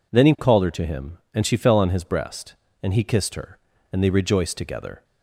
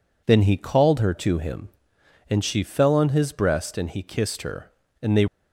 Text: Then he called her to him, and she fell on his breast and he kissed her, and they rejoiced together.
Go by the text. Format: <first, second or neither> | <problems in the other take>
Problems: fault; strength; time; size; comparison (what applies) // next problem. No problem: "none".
first | stops before "rejoiced together"; at 5.2 s